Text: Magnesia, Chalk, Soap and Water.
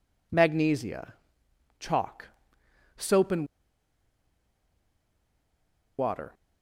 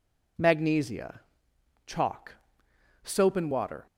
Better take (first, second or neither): second